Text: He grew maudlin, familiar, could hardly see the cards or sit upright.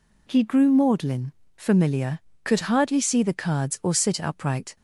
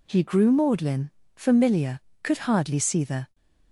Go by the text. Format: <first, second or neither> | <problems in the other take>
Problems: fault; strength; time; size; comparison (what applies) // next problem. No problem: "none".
first | stops before "cards or sit upright"; at 3.3 s